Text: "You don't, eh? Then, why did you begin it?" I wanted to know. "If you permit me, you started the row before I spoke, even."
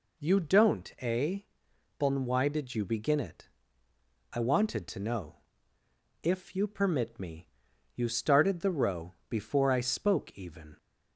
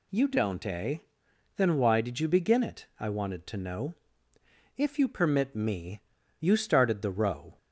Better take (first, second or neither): first